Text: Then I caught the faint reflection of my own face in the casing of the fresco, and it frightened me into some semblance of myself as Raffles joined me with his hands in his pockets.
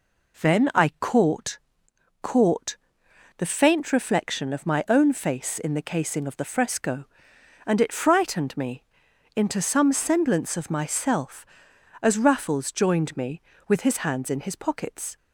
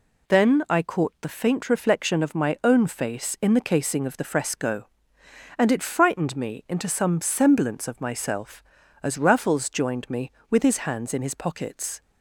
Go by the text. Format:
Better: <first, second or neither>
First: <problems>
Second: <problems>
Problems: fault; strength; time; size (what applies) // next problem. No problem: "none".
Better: second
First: says "caught" twice; at 2.2 s // pauses between "me" and "into"; noticeable; at 8.8 s; 0.54 s long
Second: none